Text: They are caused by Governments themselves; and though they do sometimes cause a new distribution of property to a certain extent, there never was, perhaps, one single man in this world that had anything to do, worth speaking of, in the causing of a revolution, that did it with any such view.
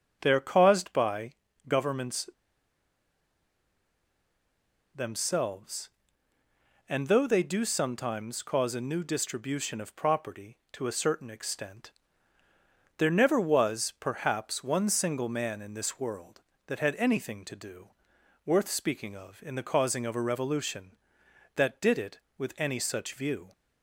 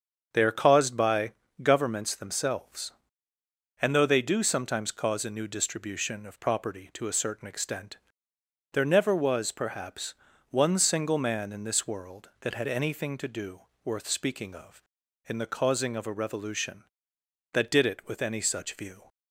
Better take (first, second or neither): second